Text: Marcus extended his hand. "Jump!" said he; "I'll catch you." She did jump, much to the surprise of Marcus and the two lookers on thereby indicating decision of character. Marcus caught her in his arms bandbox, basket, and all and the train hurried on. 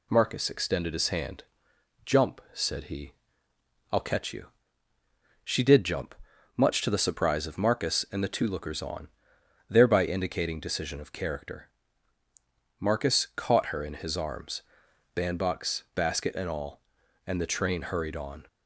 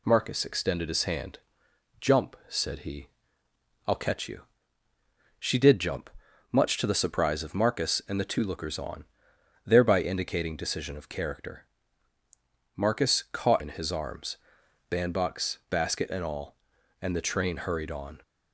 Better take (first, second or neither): first